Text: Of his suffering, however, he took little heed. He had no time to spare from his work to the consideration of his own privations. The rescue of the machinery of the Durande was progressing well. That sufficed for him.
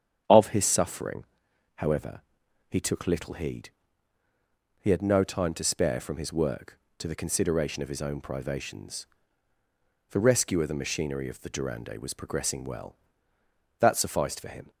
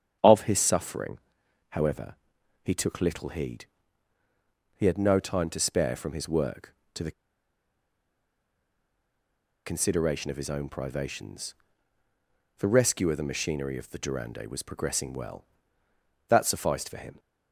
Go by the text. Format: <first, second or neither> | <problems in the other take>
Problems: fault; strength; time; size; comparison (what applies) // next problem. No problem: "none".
first | starts louder than the rest; strong; until 1.7 s; 8.5 dB; strong in the first // pauses between "the" and "consideration"; strong; at 7.1 s; 2.5 s long